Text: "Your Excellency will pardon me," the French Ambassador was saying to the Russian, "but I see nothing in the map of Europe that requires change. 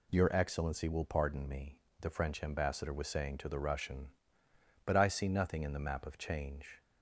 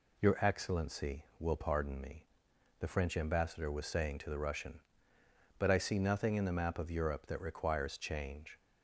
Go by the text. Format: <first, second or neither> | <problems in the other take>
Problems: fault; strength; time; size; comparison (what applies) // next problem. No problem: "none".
second | skips "Europe that requires"; at 6.1 s